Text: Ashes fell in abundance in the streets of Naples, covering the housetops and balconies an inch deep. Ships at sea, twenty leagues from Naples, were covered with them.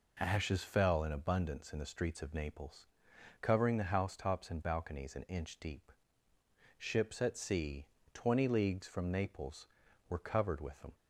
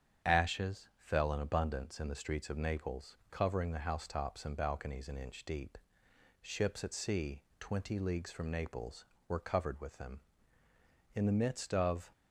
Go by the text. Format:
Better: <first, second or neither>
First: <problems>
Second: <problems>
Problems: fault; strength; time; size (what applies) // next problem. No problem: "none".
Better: first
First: none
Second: starts louder than the rest; strong; until 1.3 s; 8.5 dB // goes on to say "In the midst of"; noticeable; from 11.1 s on; 0.96 s long